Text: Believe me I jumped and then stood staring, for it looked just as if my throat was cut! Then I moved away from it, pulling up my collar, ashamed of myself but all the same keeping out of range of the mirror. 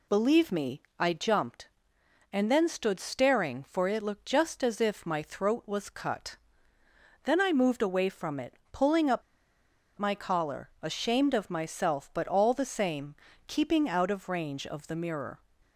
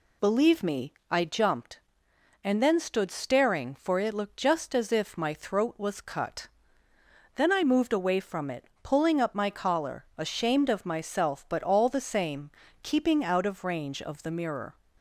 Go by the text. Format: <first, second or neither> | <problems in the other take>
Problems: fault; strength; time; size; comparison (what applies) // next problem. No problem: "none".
second | pauses between "me" and "I"; slight; at 0.8 s; 0.18 s long; slight in the second // pauses between "up" and "my"; noticeable; at 9.2 s; 0.77 s long // pauses between "same" and "keeping"; slight; at 13.1 s; 0.32 s long; slight in the second